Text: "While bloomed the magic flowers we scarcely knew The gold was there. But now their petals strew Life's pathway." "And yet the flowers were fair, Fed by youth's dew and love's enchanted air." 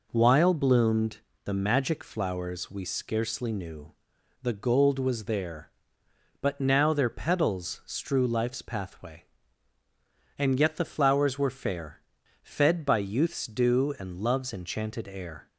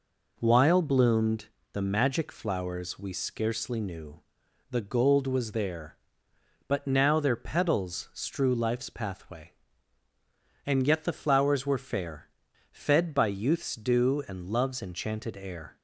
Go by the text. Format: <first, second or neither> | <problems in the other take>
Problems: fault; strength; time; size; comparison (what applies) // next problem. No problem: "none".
neither | pauses between "bloomed" and "the"; slight; the same in both // pauses between "knew" and "The"; noticeable; the same in both